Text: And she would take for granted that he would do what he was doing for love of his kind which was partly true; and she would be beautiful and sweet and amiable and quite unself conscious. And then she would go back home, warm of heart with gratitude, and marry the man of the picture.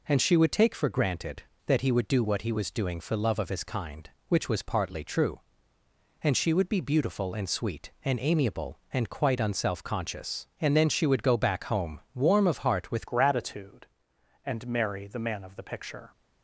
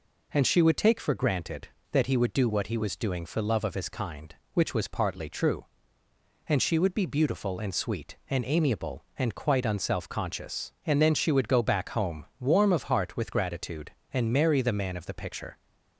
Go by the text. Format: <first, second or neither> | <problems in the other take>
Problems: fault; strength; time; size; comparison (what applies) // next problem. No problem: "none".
second | changes voice at "gratitude"; from 13.0 s on; 3.1 s long